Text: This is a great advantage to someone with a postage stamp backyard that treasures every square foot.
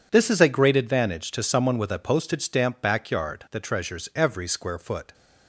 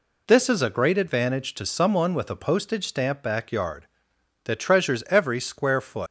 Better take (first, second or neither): first